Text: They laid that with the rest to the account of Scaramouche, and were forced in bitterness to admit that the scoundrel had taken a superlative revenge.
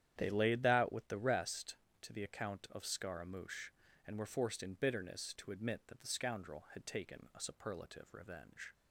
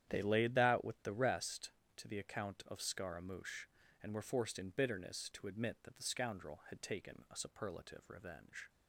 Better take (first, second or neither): neither